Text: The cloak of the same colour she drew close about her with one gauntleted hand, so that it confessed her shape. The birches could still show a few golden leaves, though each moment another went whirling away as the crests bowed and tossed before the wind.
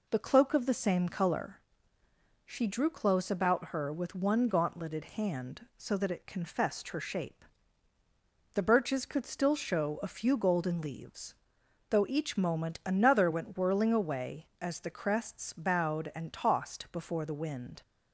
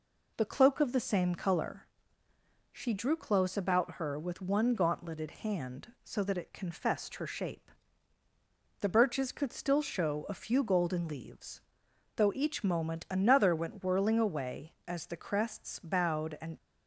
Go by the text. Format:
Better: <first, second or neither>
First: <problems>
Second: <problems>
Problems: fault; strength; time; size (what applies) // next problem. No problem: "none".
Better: first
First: pauses between "colour" and "she"; noticeable; at 1.5 s; 0.86 s long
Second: pauses between "colour" and "she"; noticeable; at 1.8 s; 0.86 s long // stops before "tossed before the wind"; at 16.5 s